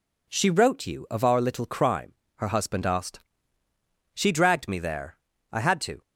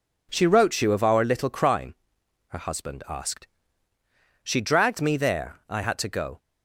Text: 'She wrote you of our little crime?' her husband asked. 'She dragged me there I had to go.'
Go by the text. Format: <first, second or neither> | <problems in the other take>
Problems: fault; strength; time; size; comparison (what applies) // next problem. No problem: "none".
second | pauses between "there" and "I"; at 5.1 s; 0.38 s long // stops before "go"; at 6.0 s